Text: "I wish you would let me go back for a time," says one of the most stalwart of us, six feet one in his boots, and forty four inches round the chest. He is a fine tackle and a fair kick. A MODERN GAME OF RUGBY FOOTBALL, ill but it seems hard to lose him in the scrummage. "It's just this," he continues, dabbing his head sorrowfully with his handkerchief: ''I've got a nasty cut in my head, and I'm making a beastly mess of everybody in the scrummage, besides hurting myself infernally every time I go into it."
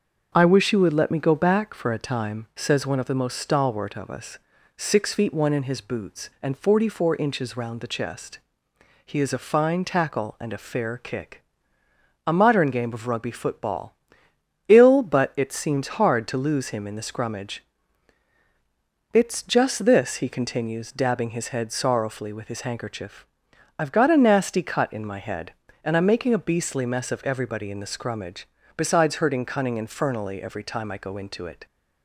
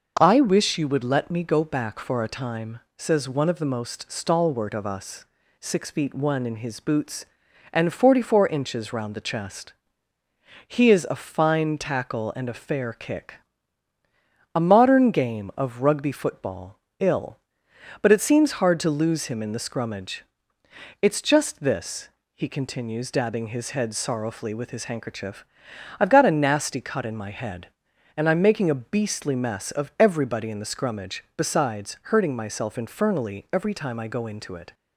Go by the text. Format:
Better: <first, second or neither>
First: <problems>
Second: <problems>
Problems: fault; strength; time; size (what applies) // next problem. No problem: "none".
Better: second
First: starts louder than the rest; until 1.3 s; 6.5 dB // says "cunning" for "myself"; at 29.4 s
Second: starts louder than the rest; noticeable; until 1.2 s; 6 dB